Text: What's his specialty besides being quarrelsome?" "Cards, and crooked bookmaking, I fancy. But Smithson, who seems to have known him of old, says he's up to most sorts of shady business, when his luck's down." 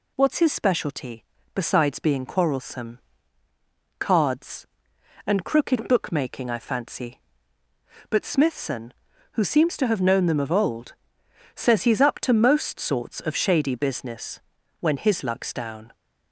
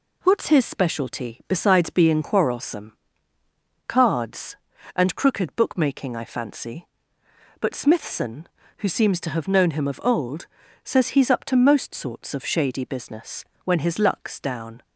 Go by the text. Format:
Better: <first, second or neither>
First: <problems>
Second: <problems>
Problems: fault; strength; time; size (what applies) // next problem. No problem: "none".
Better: second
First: pauses between "specialty" and "besides"; slight; at 1.2 s; 0.30 s long // says "them" for "him"; at 10.2 s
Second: none